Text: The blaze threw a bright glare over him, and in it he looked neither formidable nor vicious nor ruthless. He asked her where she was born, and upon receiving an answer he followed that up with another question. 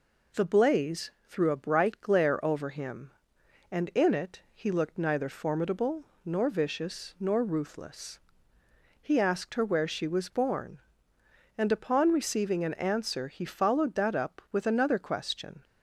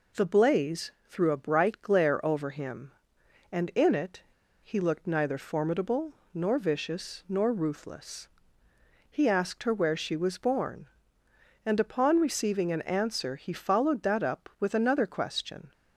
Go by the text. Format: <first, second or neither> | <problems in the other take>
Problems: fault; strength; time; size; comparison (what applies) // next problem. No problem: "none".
first | pauses between "it" and "he"; at 4.2 s; 0.42 s long // pauses between "formidable" and "nor"; slight; at 6.1 s; 0.20 s long; slight in the first